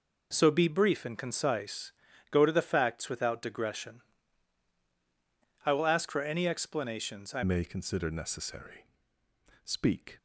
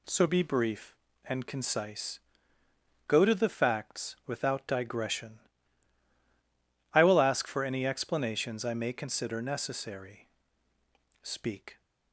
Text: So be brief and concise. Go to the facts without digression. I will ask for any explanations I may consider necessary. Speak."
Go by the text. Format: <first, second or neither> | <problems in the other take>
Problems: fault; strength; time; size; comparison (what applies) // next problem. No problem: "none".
second | changes voice at "may"; from 7.4 s on; 2.7 s long